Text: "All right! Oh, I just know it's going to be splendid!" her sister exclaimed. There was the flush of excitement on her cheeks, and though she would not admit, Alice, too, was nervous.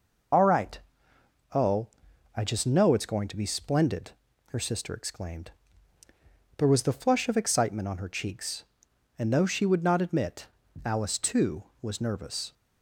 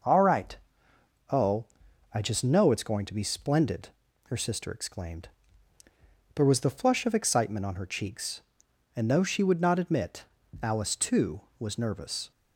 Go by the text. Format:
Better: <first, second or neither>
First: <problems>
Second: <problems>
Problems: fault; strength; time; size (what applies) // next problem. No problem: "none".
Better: second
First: loses the start of "All"; at 0.3 s; 60 ms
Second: none